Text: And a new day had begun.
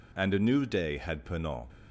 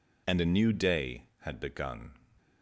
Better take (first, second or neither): second